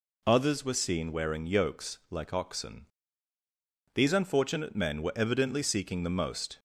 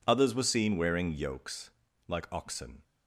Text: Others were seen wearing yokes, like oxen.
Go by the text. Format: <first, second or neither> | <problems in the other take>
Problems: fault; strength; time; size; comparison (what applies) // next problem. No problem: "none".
second | goes on to say "These unfortunate men were evidently seeking the most"; strong; from 3.9 s on; 2.6 s long